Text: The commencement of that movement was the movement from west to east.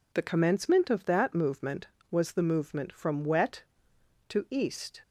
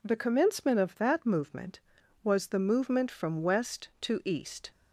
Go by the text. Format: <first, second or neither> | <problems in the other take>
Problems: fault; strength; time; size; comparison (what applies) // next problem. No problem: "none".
second | says "wet" for "west"; at 3.2 s